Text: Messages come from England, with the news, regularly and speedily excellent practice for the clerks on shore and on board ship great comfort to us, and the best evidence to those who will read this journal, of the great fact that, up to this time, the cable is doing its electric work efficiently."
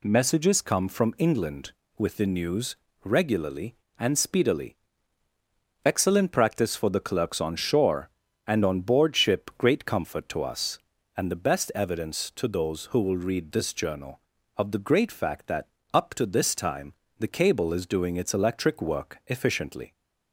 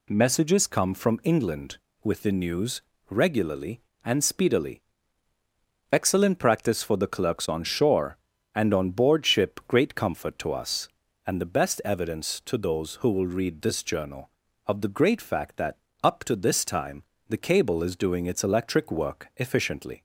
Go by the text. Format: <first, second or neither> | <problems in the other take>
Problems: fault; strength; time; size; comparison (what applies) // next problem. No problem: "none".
neither | pauses between "speedily" and "excellent"; the same in both